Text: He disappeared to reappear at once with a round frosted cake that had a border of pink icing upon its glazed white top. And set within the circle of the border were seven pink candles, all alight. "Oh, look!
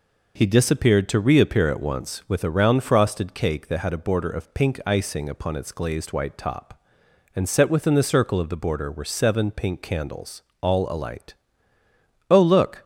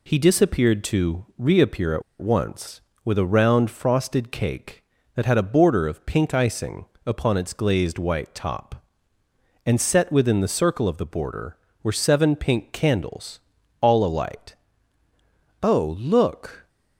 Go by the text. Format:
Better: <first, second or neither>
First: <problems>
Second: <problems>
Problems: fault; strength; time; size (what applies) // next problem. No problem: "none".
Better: first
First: none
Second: pauses between "at" and "once"; slight; at 2.0 s; 0.18 s long // pauses between "icing" and "upon"; slight; at 6.8 s; 0.20 s long